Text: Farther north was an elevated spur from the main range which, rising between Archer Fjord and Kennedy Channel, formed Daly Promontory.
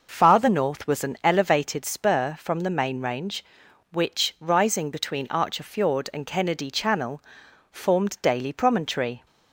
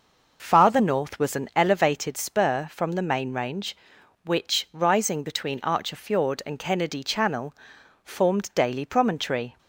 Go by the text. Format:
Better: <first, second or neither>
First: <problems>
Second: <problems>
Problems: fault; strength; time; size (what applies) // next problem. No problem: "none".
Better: neither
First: none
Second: none